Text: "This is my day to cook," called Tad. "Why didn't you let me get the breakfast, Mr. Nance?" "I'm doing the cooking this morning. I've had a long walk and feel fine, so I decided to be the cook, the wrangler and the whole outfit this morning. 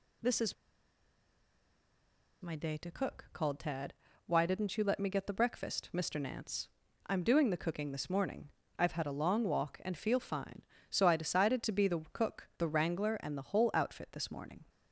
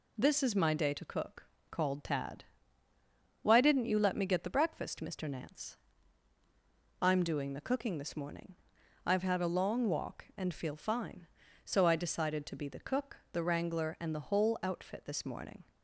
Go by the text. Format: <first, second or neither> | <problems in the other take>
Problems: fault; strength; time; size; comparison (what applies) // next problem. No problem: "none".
second | pauses between "is" and "my"; strong; at 0.5 s; 1.8 s long